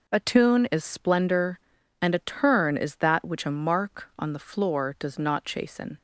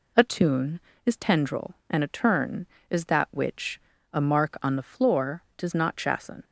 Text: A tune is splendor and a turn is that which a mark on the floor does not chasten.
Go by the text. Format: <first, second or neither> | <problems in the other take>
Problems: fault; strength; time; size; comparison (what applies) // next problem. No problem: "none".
first | says "tendril" for "splendor"; at 1.1 s // pauses between "which" and "a"; slight; at 3.7 s; 0.32 s long